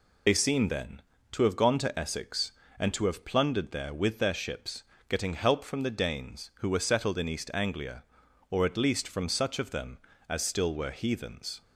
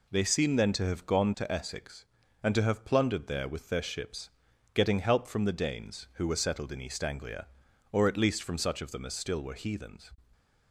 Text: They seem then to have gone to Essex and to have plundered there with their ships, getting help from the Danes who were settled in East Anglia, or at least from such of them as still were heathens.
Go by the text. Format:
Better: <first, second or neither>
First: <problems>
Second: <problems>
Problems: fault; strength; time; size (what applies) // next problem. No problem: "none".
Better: second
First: loses the start of "They"; at 0.2 s; 65 ms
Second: none